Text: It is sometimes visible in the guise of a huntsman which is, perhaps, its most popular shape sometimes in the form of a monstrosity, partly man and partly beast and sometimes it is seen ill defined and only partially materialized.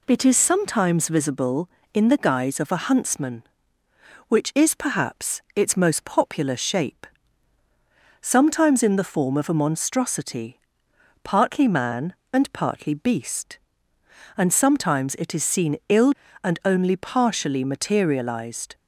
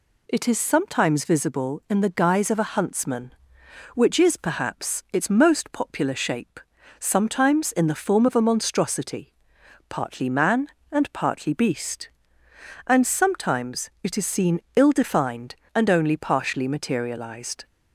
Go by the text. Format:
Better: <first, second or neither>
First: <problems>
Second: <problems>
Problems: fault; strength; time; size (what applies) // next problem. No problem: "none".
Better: second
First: pauses between "shape" and "sometimes"; at 7.0 s; 1.1 s long // skips "defined"; at 16.2 s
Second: pauses between "shape" and "sometimes"; at 6.5 s; 0.40 s long